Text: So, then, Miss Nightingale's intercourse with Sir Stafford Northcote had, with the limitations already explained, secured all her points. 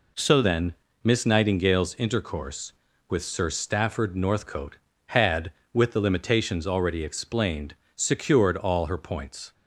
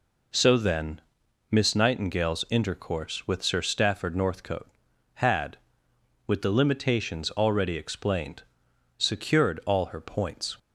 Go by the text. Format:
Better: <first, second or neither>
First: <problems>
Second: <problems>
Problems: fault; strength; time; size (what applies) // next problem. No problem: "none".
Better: second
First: changes voice at "then"; from 0.4 s on; 9.1 s long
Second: none